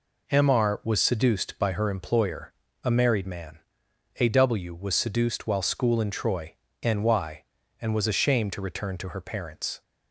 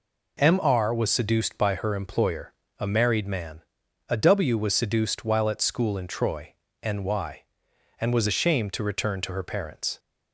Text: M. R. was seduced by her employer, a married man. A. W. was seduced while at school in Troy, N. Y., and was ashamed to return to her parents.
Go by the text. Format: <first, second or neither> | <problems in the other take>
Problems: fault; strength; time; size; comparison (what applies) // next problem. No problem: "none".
second | skips "at"; at 5.6 s